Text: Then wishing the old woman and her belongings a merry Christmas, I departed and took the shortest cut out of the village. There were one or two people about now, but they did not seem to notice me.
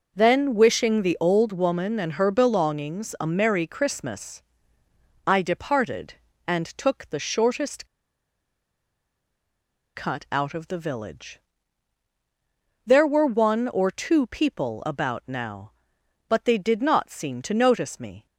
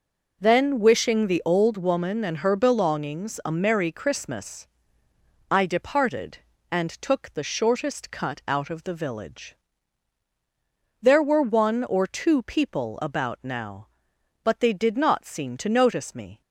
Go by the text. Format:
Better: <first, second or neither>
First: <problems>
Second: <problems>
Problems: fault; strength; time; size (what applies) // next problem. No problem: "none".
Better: second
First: pauses between "shortest" and "cut"; strong; at 7.8 s; 2.0 s long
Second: none